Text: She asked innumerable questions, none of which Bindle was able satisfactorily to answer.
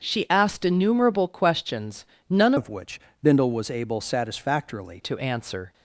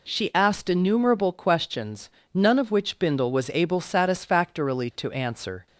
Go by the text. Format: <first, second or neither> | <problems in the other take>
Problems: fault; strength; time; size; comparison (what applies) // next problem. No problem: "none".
second | starts louder than the rest; until 1.0 s; 7 dB // changes voice from "of" to "satisfactorily"; from 2.5 to 5.0 s; 2.5 s long // pauses between "which" and "Bindle"; slight; at 3.0 s; 0.22 s long